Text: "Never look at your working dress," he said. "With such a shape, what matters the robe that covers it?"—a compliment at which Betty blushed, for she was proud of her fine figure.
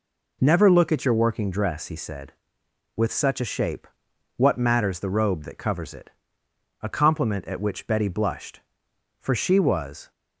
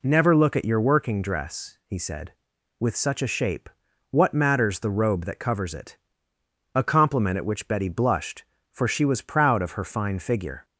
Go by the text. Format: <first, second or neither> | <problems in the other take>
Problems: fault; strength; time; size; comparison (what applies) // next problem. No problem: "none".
second | stops before "proud of her fine figure"; at 10.1 s